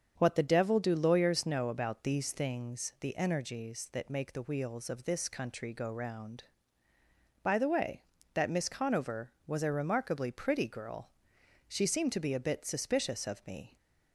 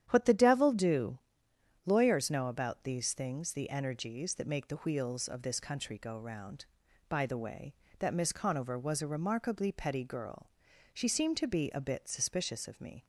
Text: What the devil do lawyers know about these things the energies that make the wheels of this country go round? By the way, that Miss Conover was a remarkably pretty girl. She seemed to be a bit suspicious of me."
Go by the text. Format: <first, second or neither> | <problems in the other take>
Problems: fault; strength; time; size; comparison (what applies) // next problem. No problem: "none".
first | starts louder than the rest; strong; until 1.1 s; 10 dB; strong in the first // pauses between "do" and "lawyers"; noticeable; at 1.1 s; 0.66 s long // says "petty" for "pretty"; at 9.7 s